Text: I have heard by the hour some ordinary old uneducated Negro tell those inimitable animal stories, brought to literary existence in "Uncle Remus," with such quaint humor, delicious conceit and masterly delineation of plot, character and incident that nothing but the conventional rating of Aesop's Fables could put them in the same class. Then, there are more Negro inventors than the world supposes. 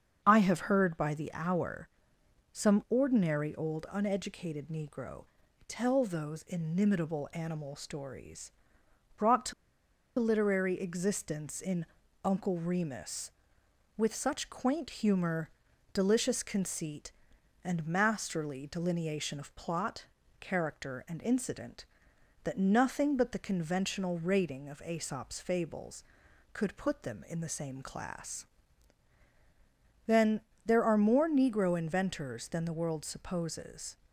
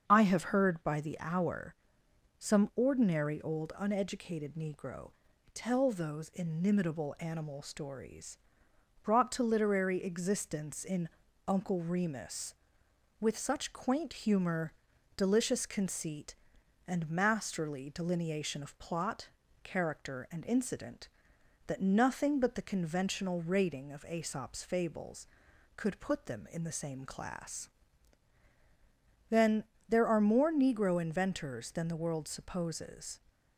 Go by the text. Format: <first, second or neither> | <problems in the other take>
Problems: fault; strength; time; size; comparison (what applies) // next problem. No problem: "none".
second | starts louder than the rest; until 1.2 s; 7 dB; also in the second // pauses between "hour" and "some"; noticeable; at 1.8 s; 0.64 s long; noticeable in the second // pauses between "Negro" and "tell"; at 5.2 s; 0.42 s long; also in the second // pauses between "to" and "literary"; noticeable; at 9.5 s; 0.66 s long // pauses between "in" and "Uncle"; at 11.8 s; 0.38 s long; also in the second